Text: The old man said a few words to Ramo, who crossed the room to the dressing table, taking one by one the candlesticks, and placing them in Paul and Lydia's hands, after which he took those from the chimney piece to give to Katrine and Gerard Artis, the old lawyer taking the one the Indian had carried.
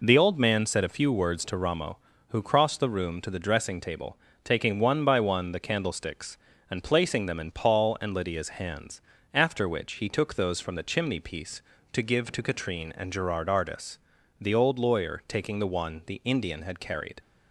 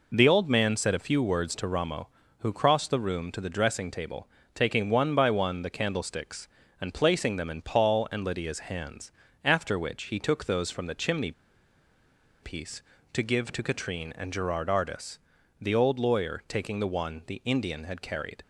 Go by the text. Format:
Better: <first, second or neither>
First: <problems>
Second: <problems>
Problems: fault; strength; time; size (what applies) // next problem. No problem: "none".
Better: first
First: none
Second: pauses between "chimney" and "piece"; at 11.3 s; 1.1 s long